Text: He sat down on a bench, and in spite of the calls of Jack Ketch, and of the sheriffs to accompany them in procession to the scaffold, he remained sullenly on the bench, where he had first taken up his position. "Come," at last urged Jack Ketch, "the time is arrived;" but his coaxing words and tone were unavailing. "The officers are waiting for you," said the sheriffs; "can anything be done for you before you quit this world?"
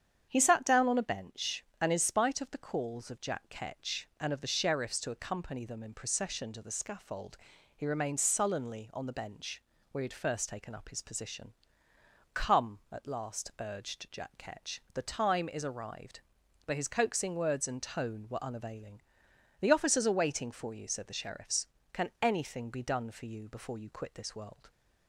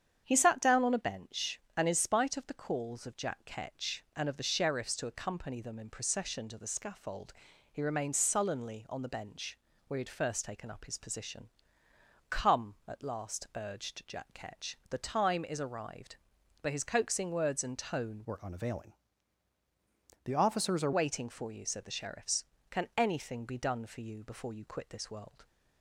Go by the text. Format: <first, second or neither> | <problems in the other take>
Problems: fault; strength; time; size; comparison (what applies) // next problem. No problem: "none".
first | starts louder than the rest; strong; until 1.2 s; 8.5 dB; strong in the first // changes voice from "were" to "are"; from 18.2 to 20.9 s; 2.7 s long